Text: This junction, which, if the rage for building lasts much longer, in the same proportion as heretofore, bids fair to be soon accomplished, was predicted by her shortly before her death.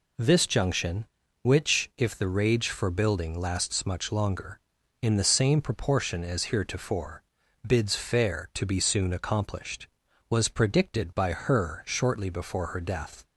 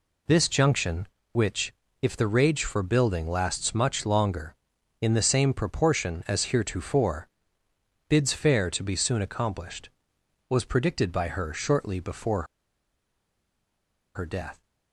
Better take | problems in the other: first | pauses between "before" and "her"; strong; at 12.4 s; 1.7 s long

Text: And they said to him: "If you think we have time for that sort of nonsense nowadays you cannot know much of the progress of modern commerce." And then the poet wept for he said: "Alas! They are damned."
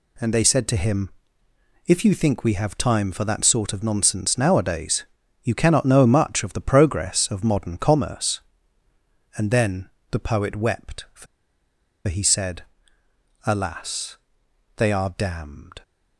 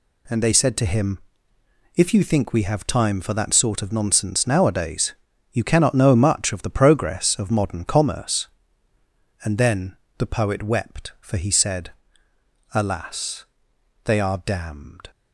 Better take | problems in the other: second | pauses between "nowadays" and "you"; at 5.0 s; 0.38 s long; also in the second // pauses between "then" and "the"; slight; at 9.8 s; 0.22 s long; slight in the second // pauses between "for" and "he"; noticeable; at 11.2 s; 0.82 s long

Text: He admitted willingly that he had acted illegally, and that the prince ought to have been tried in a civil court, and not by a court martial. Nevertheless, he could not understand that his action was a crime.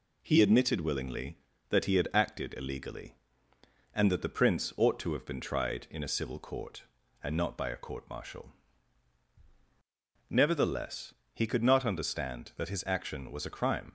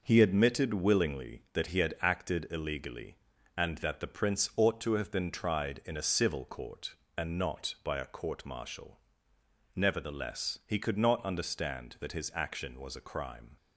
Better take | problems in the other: neither | none

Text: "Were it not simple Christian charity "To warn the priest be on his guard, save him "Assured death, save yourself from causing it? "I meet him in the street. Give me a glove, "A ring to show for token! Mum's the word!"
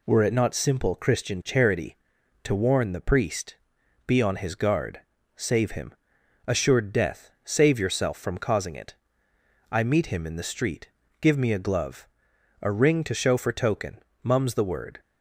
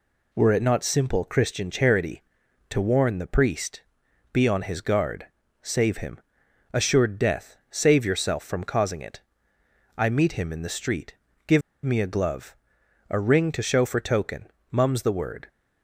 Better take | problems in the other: first | pauses between "priest" and "be"; noticeable; at 3.8 s; 0.50 s long; noticeable in the first // pauses between "him" and "Assured"; noticeable; at 6.2 s; 0.50 s long; noticeable in the first // pauses between "Give" and "me"; slight; at 11.6 s; 0.24 s long

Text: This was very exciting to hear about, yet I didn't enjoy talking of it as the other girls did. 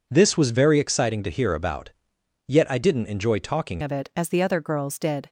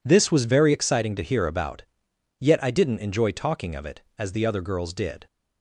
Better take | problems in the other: second | changes voice at "of"; from 3.8 s on; 1.4 s long

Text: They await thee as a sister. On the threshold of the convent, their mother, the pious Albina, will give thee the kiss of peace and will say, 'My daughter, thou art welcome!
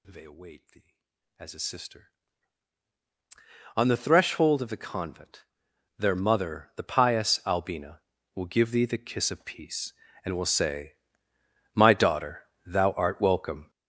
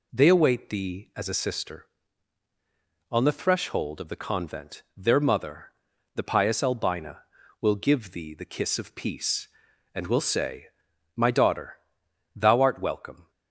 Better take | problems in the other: second | gets louder; strong; throughout; 13.5 dB

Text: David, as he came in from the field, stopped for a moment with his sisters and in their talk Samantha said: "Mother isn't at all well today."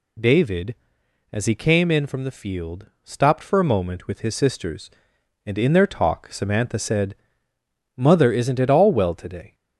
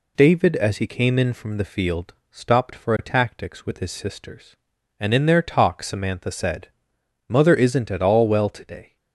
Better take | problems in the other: first | says "tactics" for "moment"; at 3.0 s

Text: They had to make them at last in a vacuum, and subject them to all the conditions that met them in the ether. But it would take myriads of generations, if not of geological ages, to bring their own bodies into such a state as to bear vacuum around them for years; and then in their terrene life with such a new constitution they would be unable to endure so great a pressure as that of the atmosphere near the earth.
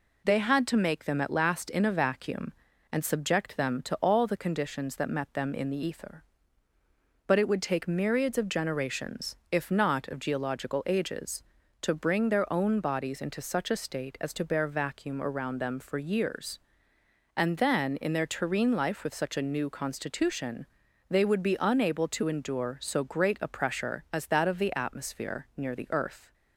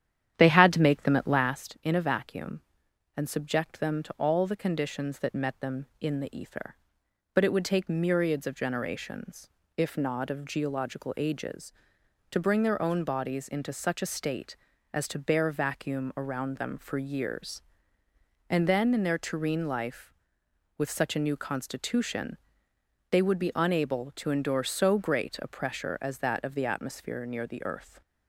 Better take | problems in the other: first | starts louder than the rest; strong; until 1.7 s; 10 dB // pauses between "constitution" and "they"; noticeable; at 22.3 s; 0.74 s long; also in the first

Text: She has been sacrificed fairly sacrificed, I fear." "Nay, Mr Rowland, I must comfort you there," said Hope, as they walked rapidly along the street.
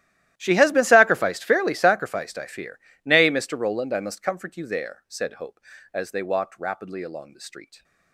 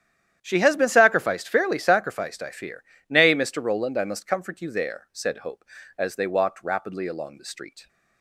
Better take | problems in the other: second | gets quieter; strong; throughout; 22 dB // starts louder than the rest; strong; until 1.3 s; 13.5 dB; strong in the second

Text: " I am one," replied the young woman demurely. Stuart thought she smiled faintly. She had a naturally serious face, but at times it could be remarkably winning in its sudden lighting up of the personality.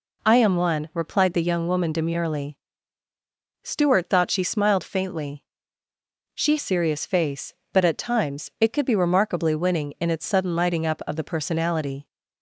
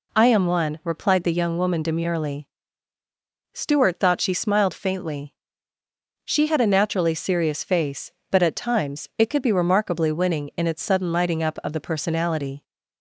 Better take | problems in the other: second | skips "had a naturally"; at 6.5 s

